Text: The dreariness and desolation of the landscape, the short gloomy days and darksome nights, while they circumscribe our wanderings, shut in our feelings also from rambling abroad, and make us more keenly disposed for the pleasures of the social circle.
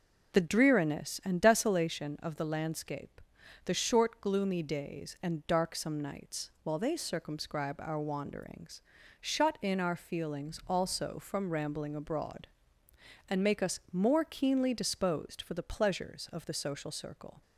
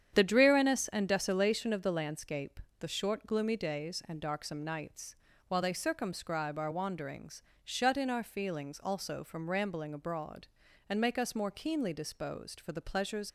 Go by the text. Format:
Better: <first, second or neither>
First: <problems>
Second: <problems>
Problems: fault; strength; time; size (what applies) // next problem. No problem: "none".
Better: first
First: none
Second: starts louder than the rest; strong; until 1.2 s; 9 dB // stops before "of the social circle"; at 13.2 s